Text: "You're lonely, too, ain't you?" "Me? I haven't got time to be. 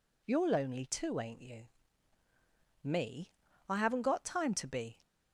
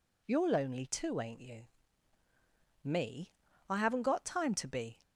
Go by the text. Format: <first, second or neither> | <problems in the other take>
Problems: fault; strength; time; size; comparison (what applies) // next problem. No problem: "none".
neither | none